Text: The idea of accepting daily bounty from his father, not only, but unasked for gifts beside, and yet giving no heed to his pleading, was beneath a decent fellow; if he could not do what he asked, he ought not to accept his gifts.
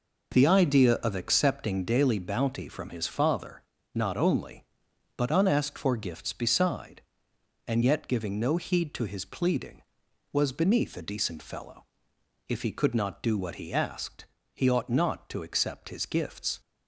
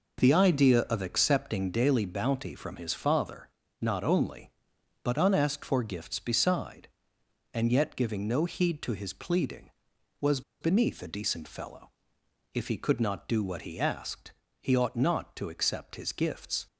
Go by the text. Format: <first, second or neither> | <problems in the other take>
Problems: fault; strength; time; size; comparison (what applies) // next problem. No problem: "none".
first | pauses between "was" and "beneath"; slight; at 10.4 s; 0.19 s long